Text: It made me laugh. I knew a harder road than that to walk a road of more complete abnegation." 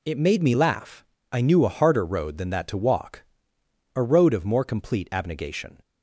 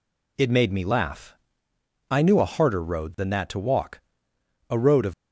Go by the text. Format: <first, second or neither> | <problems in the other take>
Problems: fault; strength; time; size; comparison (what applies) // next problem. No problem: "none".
first | pauses between "walk" and "a"; noticeable; at 3.9 s; 0.70 s long; noticeable in the first // stops before "more complete abnegation"; at 5.1 s